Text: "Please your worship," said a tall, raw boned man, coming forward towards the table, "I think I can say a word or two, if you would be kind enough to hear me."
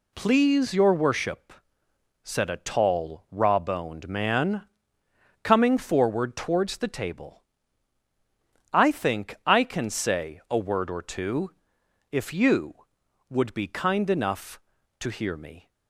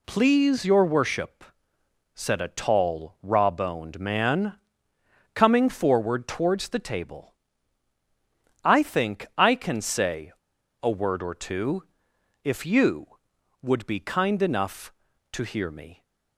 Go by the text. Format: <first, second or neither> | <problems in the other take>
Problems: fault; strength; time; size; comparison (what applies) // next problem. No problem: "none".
first | pauses between "say" and "a"; noticeable; at 10.3 s; 0.50 s long